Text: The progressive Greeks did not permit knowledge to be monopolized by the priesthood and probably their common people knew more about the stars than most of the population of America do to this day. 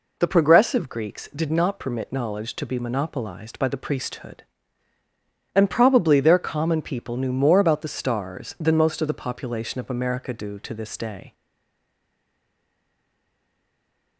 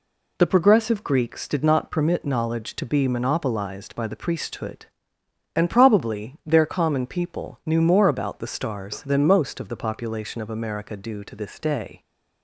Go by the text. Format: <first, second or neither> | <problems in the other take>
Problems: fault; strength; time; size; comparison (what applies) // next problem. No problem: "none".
second | stays silent after the last word; strong; from 11.3 s on; 2.8 s long